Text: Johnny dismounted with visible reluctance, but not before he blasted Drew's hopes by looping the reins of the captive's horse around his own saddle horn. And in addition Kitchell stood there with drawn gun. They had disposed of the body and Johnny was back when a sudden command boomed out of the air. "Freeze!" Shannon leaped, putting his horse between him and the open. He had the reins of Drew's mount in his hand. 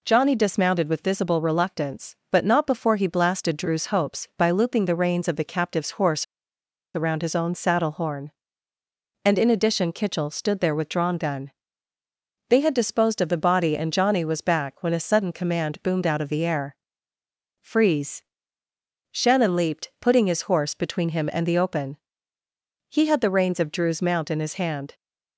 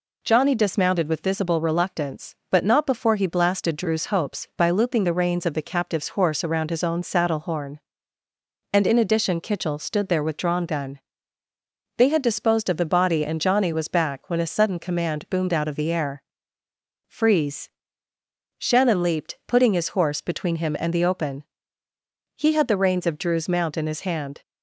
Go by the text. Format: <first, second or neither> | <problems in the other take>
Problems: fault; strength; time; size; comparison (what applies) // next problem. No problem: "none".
second | pauses between "horse" and "around"; noticeable; at 6.2 s; 0.70 s long